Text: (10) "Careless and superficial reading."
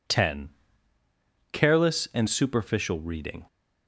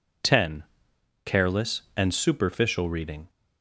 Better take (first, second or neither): neither